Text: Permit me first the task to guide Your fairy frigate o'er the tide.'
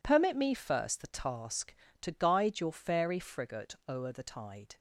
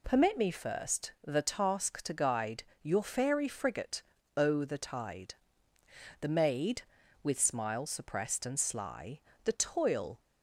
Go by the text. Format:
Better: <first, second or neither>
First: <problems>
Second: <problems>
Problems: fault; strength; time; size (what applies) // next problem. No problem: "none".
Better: first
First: none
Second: pauses between "guide" and "Your"; slight; at 2.6 s; 0.20 s long // pauses between "frigate" and "o'er"; slight; at 4.0 s; 0.34 s long // goes on to say "The maid with smile suppressed and sly The toil"; strong; from 6.2 s on; 3.9 s long